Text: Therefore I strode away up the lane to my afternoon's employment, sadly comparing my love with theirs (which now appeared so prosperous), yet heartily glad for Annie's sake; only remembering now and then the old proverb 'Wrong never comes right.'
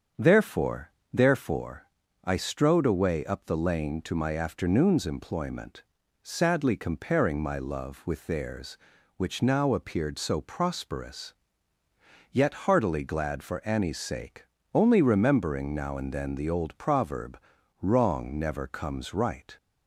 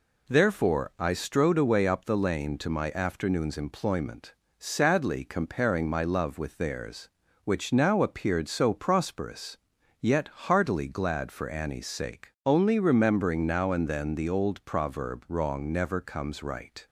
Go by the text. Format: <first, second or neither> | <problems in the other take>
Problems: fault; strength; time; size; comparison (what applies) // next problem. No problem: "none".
second | starts louder than the rest; strong; until 1.3 s; 7 dB // says "Therefore" twice; at 1.1 s // pauses between "proverb" and "Wrong"; at 17.3 s; 0.44 s long